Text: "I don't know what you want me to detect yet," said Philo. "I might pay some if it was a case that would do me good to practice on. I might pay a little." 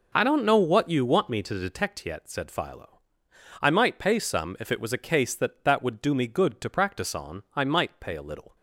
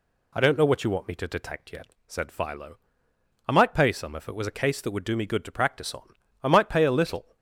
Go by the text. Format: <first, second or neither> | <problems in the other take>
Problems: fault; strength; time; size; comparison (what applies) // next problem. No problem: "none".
second | says "that" twice; at 5.6 s